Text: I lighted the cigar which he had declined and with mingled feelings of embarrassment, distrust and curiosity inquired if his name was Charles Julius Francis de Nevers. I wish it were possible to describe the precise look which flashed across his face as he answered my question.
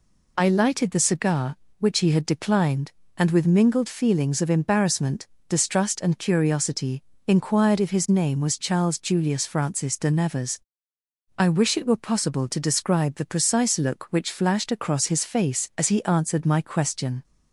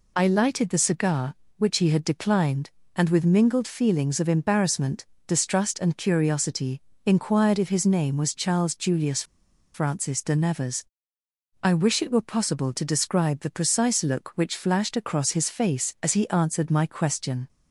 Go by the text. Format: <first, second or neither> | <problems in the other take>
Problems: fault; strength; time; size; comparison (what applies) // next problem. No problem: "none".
first | pauses between "curiosity" and "inquired"; slight; at 6.8 s; 0.24 s long; slight in the first // pauses between "Julius" and "Francis"; noticeable; at 9.2 s; 0.50 s long